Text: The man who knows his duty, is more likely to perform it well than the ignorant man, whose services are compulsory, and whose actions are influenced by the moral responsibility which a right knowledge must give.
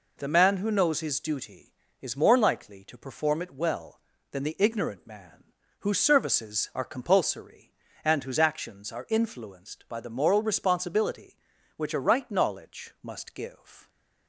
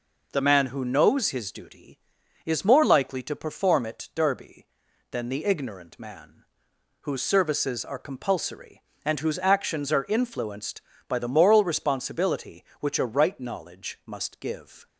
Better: first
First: none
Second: says "derby" for "well"; at 4.1 s

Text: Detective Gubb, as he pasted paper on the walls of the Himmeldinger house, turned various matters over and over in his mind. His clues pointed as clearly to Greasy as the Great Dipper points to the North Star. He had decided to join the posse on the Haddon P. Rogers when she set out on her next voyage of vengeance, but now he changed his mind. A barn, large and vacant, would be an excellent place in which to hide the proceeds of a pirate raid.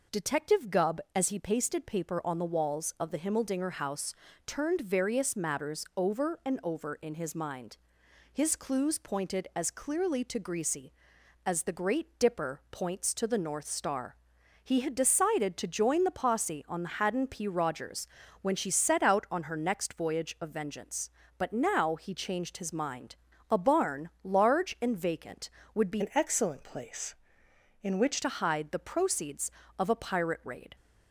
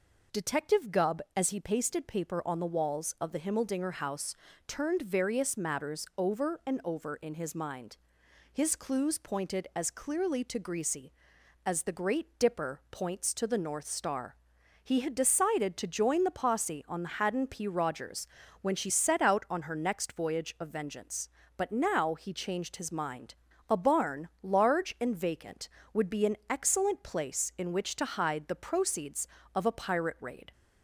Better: second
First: pauses between "Rogers" and "when"; slight; at 18.0 s; 0.34 s long // changes voice from "an" to "which"; from 26.0 to 28.2 s; 2.2 s long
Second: pauses between "Rogers" and "when"; slight; at 18.2 s; 0.34 s long

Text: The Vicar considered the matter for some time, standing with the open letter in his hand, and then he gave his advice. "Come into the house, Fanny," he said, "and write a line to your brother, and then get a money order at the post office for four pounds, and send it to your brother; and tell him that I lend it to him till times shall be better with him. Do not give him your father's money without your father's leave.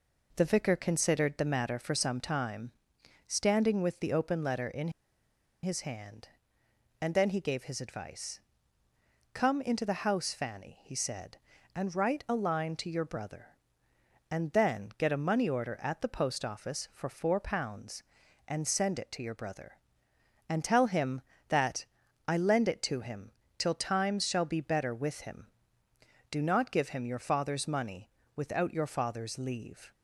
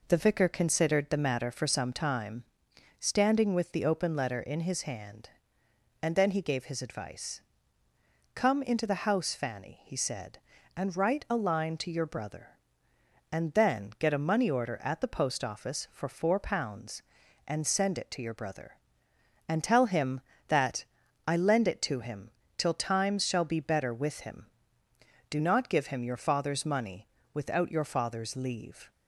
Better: second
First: pauses between "in" and "his"; noticeable; at 4.8 s; 0.73 s long // pauses between "that" and "I"; at 21.8 s; 0.44 s long // pauses between "him" and "till"; slight; at 23.3 s; 0.26 s long // pauses between "money" and "without"; slight; at 28.0 s; 0.28 s long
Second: pauses between "that" and "I"; at 20.8 s; 0.44 s long // pauses between "him" and "till"; slight; at 22.3 s; 0.26 s long // pauses between "money" and "without"; slight; at 27.0 s; 0.28 s long

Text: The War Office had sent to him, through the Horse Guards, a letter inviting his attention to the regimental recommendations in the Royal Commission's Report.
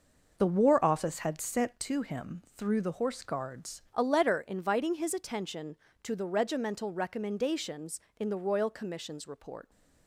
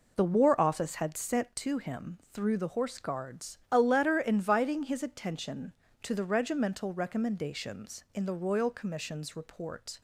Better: second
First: changes voice at "a"; from 3.9 s on; 5.7 s long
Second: none

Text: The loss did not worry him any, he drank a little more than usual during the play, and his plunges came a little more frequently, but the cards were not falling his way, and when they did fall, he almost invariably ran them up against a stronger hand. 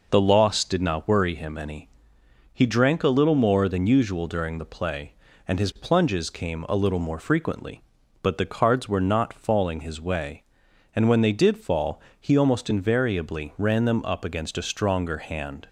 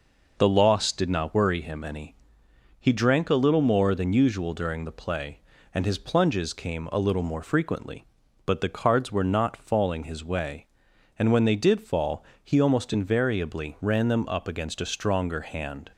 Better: neither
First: none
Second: none

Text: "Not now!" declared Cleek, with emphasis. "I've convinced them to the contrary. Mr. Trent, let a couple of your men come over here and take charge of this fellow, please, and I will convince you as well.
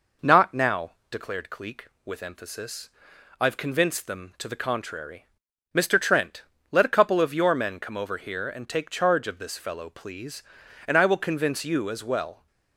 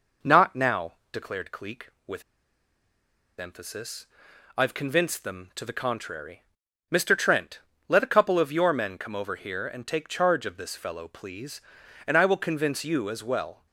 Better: first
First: none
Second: pauses between "with" and "emphasis"; at 2.2 s; 1.1 s long

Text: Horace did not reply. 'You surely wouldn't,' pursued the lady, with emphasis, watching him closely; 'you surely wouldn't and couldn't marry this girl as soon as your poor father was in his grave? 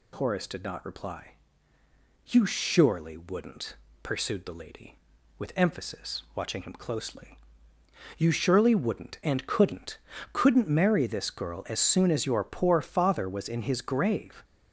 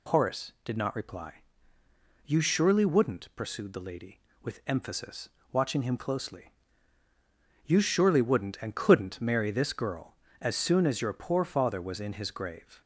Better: second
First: says "couldn't" twice; at 10.3 s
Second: none

